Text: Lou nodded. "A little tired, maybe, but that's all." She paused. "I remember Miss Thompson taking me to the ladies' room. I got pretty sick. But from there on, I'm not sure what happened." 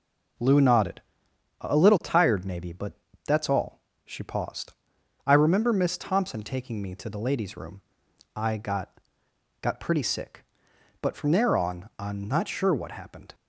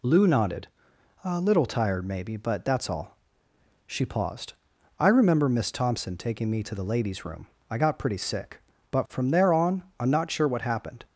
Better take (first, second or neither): second